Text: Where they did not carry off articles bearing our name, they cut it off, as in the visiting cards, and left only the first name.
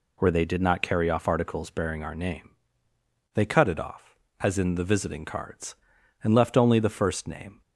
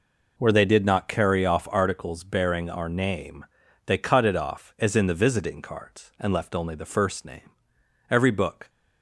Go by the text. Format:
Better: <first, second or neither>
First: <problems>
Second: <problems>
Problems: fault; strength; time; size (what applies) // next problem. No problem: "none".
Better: first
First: none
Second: goes on to say "Every book"; from 8.0 s on; 0.60 s long